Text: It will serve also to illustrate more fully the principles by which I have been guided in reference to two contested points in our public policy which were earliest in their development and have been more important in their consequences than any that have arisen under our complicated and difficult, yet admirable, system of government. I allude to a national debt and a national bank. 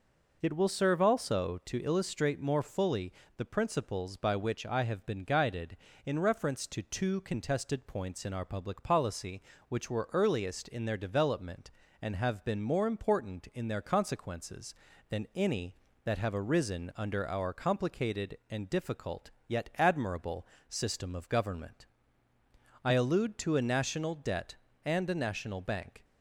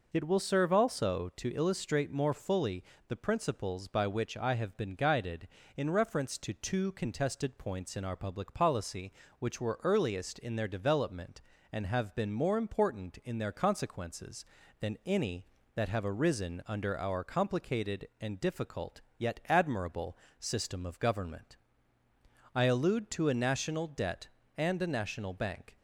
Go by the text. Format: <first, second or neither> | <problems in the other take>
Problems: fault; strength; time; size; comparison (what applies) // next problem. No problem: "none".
neither | pauses between "fully" and "the"; slight; the same in both